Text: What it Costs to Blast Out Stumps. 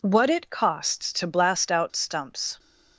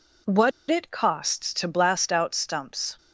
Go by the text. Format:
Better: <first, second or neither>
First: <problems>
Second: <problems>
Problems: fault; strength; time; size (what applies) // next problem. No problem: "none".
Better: first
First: none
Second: pauses between "What" and "it"; slight; at 0.5 s; 0.19 s long